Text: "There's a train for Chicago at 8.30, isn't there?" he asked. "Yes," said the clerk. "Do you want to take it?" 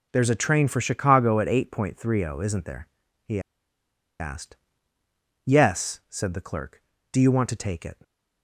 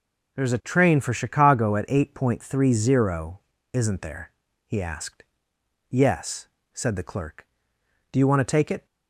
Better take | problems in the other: second | pauses between "he" and "asked"; noticeable; at 3.3 s; 0.80 s long

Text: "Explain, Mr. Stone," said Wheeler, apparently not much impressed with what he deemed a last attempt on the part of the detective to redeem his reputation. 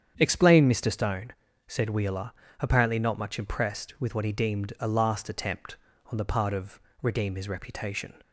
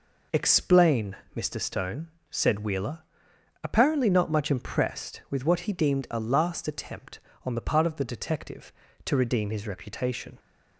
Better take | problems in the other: second | starts louder than the rest; strong; until 1.1 s; 8 dB // skips "the detective to"; at 6.9 s

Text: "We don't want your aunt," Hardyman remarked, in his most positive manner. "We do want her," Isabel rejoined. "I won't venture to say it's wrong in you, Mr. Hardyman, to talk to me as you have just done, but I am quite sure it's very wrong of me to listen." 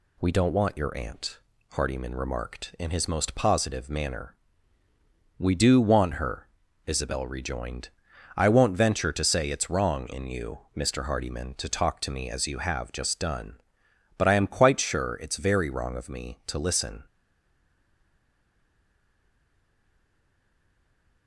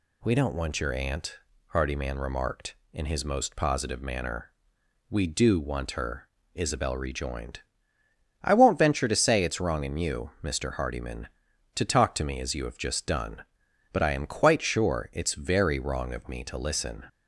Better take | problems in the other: second | stays silent after the last word; strong; from 17.0 s on; 4.2 s long

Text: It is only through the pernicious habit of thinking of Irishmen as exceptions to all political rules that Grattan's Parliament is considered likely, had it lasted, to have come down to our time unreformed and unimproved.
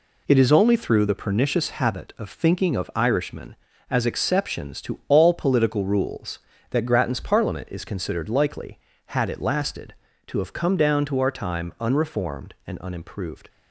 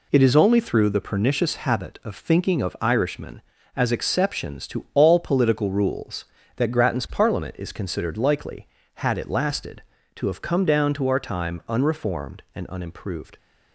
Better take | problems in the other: neither | none

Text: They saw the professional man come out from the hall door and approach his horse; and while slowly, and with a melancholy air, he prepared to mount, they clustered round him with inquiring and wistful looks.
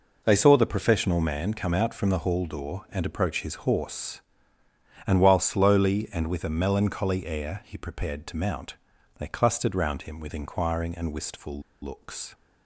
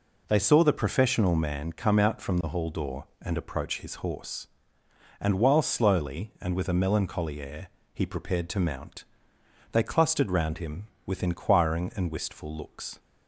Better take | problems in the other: second | pauses between "wistful" and "looks"; slight; at 11.6 s; 0.21 s long

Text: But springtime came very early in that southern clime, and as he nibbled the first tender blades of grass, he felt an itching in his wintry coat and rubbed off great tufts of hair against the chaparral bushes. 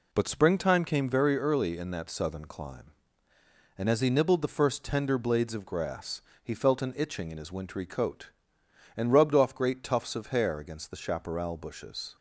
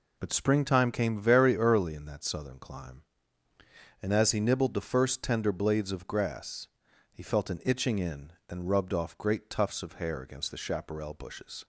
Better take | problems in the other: first | skips "his wintry coat"; at 8.4 s

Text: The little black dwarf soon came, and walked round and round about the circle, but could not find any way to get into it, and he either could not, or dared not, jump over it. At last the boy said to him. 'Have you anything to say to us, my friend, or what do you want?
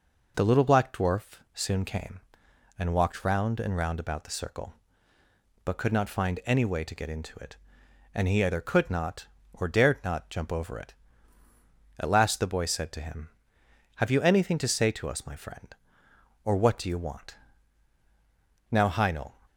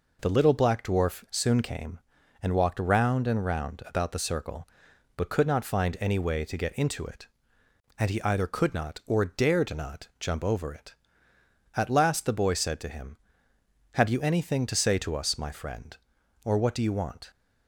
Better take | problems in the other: second | goes on to say "Now Heinel"; noticeable; from 18.6 s on; 0.66 s long

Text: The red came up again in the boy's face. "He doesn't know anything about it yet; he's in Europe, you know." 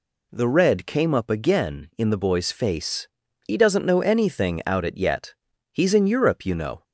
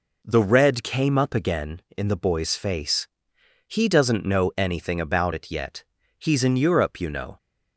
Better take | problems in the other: second | says "out" for "about"; at 4.6 s

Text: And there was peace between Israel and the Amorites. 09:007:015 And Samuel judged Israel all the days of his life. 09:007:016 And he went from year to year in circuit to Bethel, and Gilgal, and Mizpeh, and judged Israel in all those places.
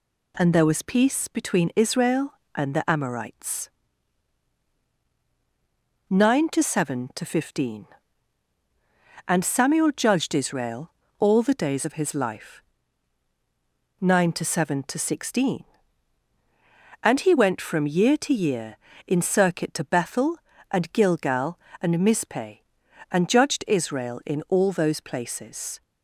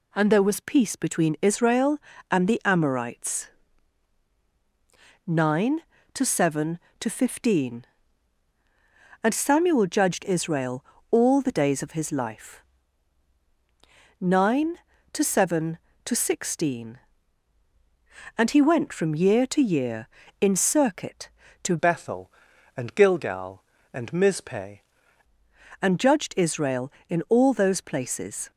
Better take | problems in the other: first | pauses between "Israel" and "all"; slight; at 10.8 s; 0.26 s long; slight in the first // changes voice from "Bethel" to "Mizpeh"; from 21.7 to 24.8 s; 3.1 s long

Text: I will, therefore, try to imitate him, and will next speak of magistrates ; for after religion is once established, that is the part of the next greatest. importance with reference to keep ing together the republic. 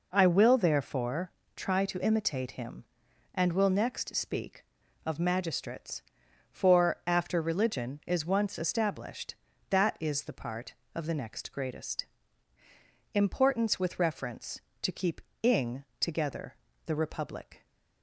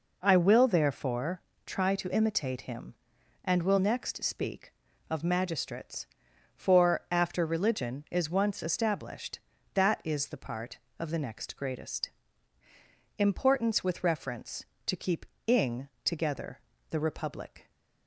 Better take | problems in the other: neither | pauses between "keep" and "ing"; slight; the same in both // pauses between "ing" and "together"; slight; the same in both // pauses between "together" and "the"; slight; the same in both

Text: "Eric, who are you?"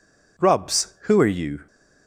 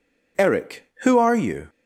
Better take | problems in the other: second | says "Rubs" for "Eric"; at 0.3 s

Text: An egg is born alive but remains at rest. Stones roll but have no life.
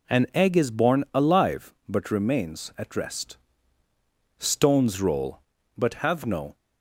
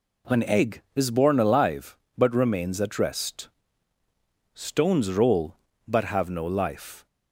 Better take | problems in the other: second | stops before "life"; at 6.5 s

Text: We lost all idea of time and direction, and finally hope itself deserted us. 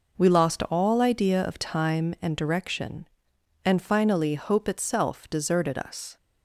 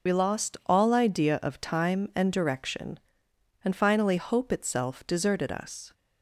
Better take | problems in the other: first | loses the start of "We"; at 0.0 s; 45 ms

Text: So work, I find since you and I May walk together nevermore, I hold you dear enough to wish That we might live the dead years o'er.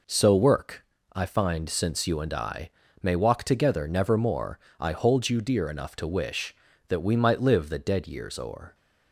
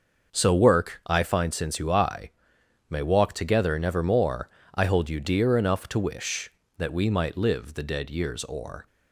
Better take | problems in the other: first | starts louder than the rest; until 1.4 s; 6 dB // skips "and"; at 1.8 s // pauses between "I" and "May"; noticeable; at 2.2 s; 0.58 s long; slight in the first

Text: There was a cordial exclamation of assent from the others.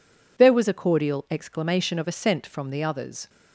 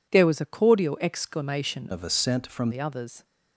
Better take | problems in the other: first | changes voice from "of" to "from"; from 1.9 to 2.7 s; 0.8 s long

